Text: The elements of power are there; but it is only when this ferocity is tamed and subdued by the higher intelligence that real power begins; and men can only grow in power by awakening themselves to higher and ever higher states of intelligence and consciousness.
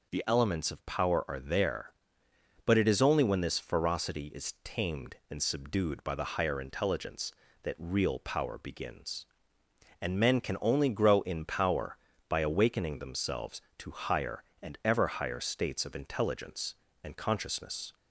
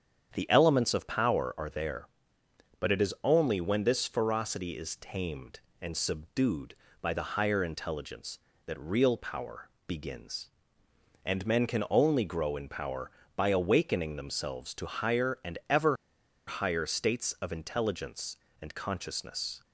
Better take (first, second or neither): first